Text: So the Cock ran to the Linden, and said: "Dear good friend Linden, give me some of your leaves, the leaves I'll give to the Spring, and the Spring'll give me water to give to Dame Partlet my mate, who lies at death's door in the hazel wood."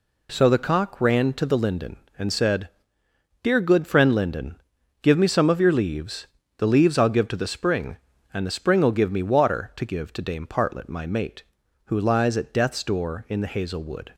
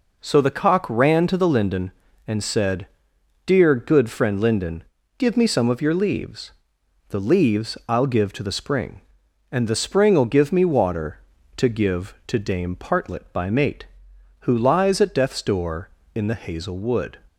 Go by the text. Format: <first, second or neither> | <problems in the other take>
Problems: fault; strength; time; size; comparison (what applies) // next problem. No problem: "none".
first | says "by" for "my"; at 13.3 s